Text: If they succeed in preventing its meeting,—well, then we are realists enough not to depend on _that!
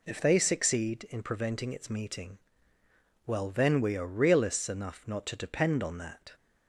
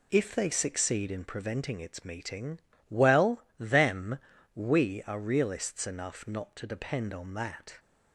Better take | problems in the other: first | says "them" for "then"; at 3.5 s

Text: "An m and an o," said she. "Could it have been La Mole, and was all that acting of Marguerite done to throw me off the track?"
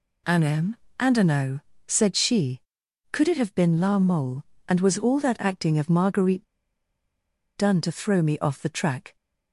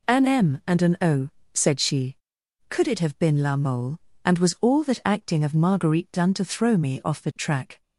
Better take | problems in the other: second | pauses between "Marguerite" and "done"; at 6.4 s; 1.1 s long

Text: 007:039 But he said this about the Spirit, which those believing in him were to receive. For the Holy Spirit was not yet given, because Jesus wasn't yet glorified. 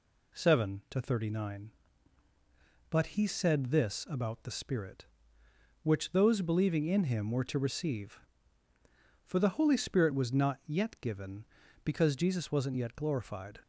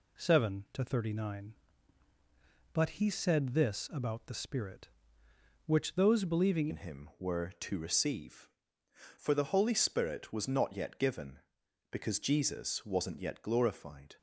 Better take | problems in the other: first | changes voice at "in"; from 6.6 s on; 7.5 s long

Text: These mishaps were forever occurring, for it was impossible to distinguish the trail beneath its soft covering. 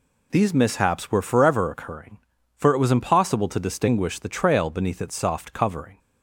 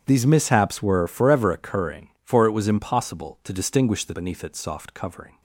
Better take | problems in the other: first | starts louder than the rest; strong; until 1.0 s; 9 dB // skips "trail"; at 4.1 s

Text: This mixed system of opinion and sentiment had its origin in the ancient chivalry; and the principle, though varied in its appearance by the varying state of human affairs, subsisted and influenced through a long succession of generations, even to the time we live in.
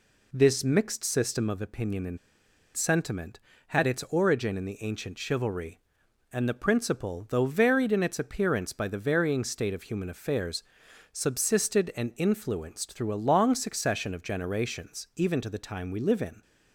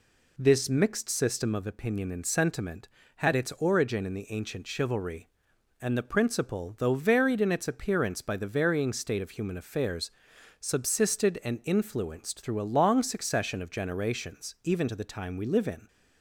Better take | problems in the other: second | pauses between "and" and "sentiment"; noticeable; at 2.1 s; 0.59 s long

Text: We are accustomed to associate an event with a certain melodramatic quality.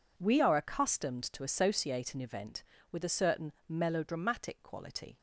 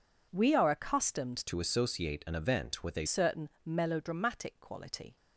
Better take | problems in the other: first | changes voice from "to" to "a"; from 1.4 to 3.0 s; 1.6 s long // pauses between "certain" and "melodramatic"; slight; at 3.4 s; 0.16 s long; slight in the first

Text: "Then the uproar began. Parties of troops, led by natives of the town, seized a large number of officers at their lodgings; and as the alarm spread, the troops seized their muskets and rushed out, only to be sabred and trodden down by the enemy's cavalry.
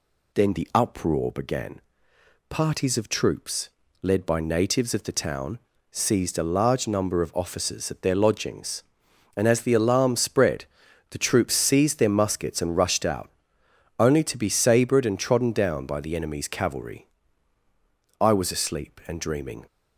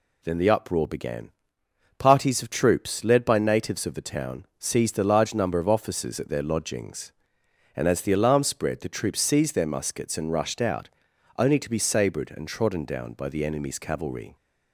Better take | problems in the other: second | goes on to say "I was asleep and dreaming"; from 18.2 s on; 1.4 s long

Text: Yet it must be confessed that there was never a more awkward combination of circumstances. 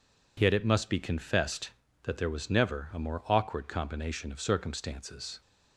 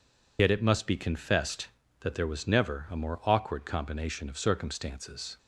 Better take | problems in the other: first | loses the start of "Yet"; at 0.3 s; 50 ms

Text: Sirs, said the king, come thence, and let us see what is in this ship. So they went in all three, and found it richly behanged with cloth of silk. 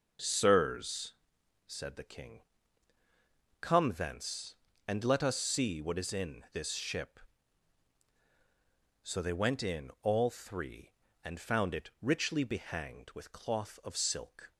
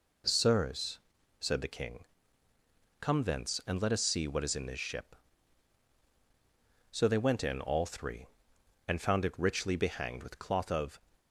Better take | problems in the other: first | stops before "silk"; at 11.1 s

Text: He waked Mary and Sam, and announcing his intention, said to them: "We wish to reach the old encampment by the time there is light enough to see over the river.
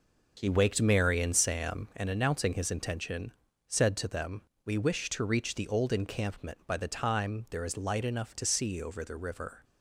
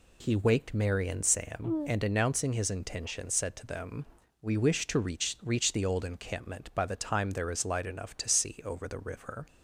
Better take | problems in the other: first | says "reach" twice; at 5.4 s

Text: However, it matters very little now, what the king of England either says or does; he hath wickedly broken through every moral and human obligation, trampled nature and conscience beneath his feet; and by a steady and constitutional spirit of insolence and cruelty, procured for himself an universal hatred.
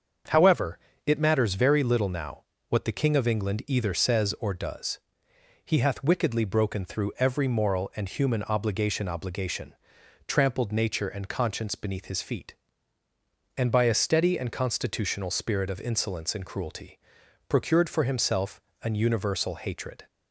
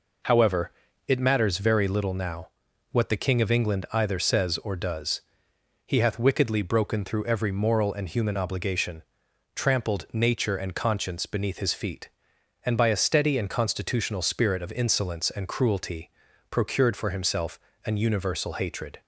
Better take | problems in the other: second | starts louder than the rest; until 1.5 s; 7 dB // says "obligation" twice; at 9.0 s // pauses between "himself" and "an"; slight; at 18.6 s; 0.22 s long; slight in the second

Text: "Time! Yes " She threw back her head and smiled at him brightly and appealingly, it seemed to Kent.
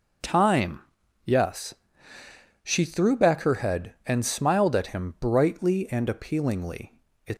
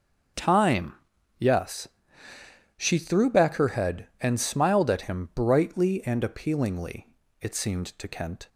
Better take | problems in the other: second | stops before "seemed to Kent"; at 7.3 s

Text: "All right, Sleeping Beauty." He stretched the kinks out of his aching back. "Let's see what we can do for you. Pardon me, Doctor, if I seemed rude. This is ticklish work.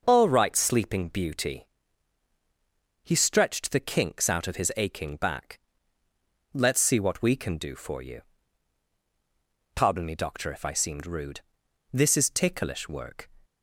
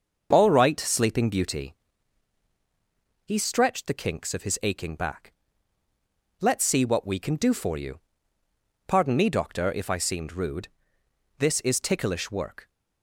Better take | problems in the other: first | starts louder than the rest; until 1.3 s; 6.5 dB // skips "out"; at 4.3 s

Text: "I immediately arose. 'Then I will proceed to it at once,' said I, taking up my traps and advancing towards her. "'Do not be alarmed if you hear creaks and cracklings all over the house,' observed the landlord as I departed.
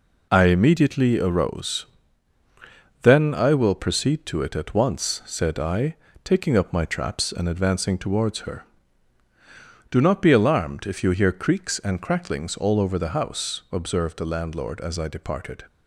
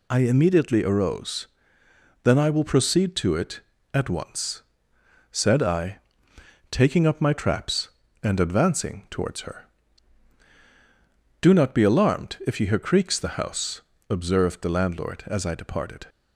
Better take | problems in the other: first | skips "and cracklings all over"; at 13.1 s

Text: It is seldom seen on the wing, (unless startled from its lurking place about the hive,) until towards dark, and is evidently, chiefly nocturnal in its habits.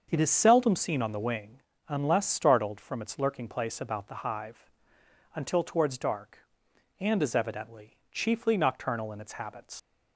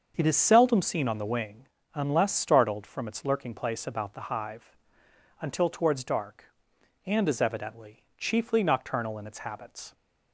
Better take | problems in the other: second | starts louder than the rest; until 1.1 s; 6.5 dB; also in the second // leaves "habits" unfinished; at 9.7 s; 75 ms

